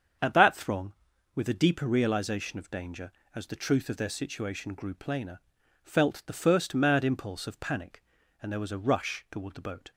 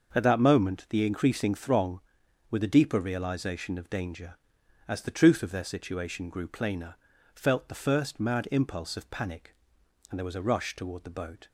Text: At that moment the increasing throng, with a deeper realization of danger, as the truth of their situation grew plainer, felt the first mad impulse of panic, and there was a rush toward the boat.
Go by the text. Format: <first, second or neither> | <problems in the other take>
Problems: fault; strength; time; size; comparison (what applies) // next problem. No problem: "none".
second | starts louder than the rest; strong; until 1.6 s; 7.5 dB; also in the second // skips "moment the increasing"; at 0.5 s